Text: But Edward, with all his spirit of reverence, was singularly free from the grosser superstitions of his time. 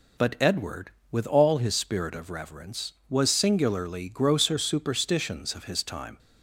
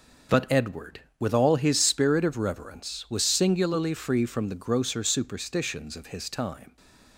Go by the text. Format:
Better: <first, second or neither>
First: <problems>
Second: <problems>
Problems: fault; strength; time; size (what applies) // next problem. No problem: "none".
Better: second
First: skips "free from the"; at 4.0 s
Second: none